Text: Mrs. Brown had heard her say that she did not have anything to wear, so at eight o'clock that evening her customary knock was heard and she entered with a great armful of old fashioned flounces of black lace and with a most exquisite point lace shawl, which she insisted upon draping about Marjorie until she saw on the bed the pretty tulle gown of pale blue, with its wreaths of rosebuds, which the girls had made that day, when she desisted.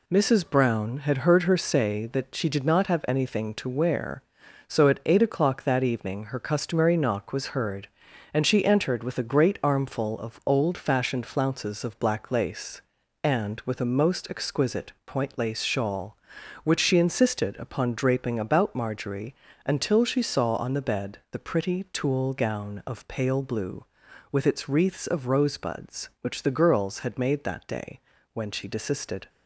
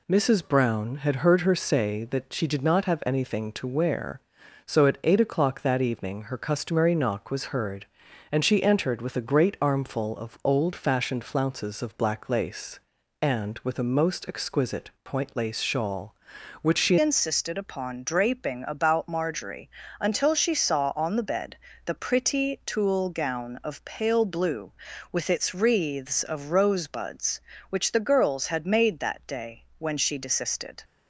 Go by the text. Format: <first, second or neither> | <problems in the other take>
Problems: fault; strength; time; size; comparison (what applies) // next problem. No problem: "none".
first | pauses between "exquisite" and "point"; slight; at 14.8 s; 0.16 s long; slight in the first // changes voice at "insisted"; from 17.0 s on; 13.8 s long // pauses between "Marjorie" and "until"; slight; at 19.6 s; 0.30 s long; slight in the first // pauses between "bed" and "the"; slight; at 21.5 s; 0.30 s long